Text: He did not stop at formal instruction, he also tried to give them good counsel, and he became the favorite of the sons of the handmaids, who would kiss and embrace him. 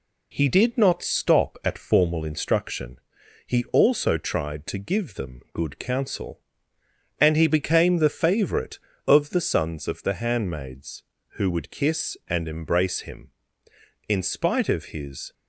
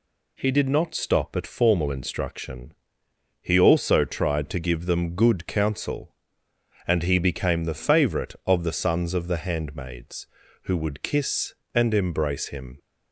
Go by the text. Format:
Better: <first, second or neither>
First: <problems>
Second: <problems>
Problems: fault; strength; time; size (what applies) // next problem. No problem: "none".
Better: second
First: goes on to say "In spite of his"; noticeable; from 14.0 s on; 1.2 s long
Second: none